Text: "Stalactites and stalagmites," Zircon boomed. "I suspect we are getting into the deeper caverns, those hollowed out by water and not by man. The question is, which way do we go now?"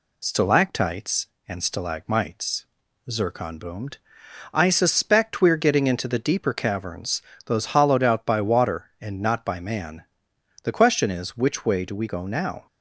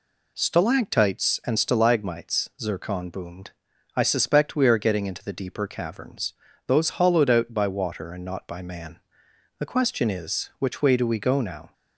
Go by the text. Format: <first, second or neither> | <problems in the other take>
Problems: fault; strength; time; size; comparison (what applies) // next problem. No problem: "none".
neither | none